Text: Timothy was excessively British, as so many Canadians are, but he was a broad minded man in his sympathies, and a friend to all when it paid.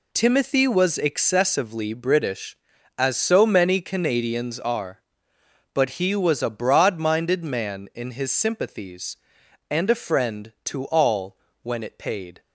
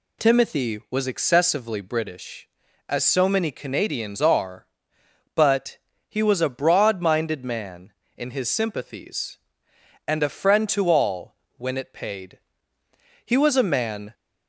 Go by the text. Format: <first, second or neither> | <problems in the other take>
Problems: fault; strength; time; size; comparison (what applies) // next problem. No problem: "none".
first | pauses between "but" and "he"; slight; at 5.7 s; 0.32 s long // pauses between "all" and "when"; slight; at 11.3 s; 0.20 s long; slight in the first // goes on to say "He was a man"; noticeable; from 13.2 s on; 0.88 s long